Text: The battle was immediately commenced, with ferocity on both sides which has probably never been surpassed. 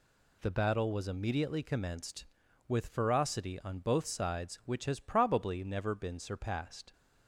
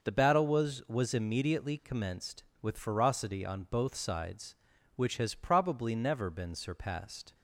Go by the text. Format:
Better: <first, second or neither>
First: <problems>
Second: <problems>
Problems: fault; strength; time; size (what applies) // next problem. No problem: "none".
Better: first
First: none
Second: says "was" twice; at 0.8 s